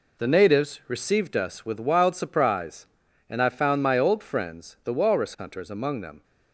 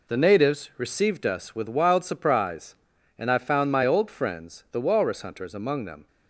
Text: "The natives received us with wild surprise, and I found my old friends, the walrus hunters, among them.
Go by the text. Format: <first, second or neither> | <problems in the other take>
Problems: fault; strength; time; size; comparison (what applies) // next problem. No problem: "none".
neither | none